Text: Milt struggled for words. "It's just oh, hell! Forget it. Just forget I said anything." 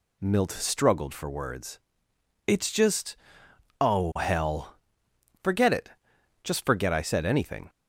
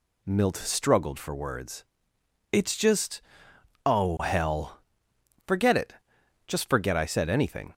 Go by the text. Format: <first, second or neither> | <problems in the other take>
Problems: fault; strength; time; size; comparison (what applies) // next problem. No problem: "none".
neither | pauses between "just" and "oh"; noticeable; the same in both